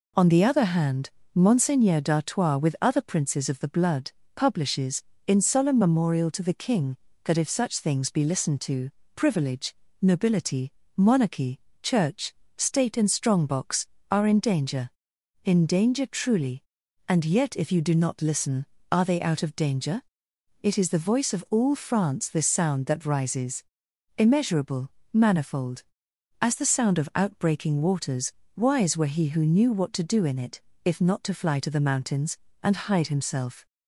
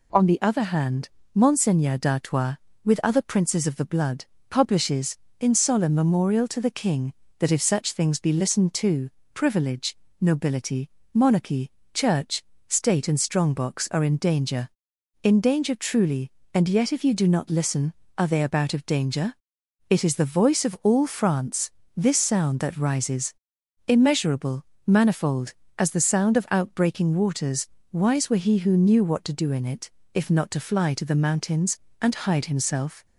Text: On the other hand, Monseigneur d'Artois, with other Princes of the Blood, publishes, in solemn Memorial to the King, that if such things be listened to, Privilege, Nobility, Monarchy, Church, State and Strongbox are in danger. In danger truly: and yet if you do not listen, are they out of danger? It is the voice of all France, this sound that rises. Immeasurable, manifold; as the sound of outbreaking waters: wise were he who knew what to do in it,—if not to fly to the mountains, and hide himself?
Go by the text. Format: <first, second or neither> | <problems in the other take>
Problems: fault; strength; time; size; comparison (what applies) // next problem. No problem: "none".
first | says "about" for "out"; at 18.4 s